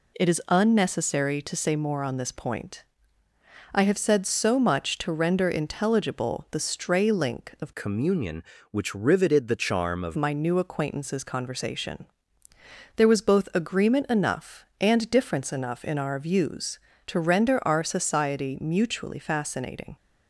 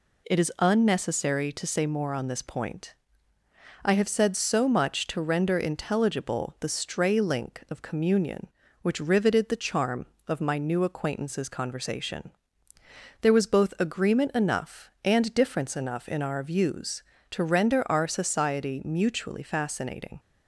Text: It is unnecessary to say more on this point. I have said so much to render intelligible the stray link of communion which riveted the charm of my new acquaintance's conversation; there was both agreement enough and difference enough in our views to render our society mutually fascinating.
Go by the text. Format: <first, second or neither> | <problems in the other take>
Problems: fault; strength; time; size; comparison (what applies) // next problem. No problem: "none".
second | changes voice from "communion" to "of"; from 7.7 to 10.1 s; 2.4 s long